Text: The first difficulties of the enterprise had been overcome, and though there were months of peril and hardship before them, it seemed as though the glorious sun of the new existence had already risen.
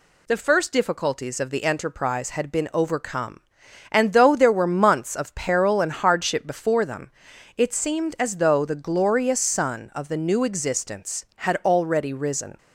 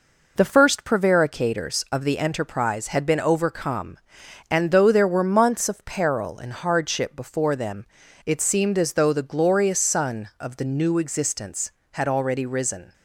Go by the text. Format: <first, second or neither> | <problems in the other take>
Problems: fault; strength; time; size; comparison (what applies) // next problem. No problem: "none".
first | says "prevaricators" for "difficulties"; at 0.8 s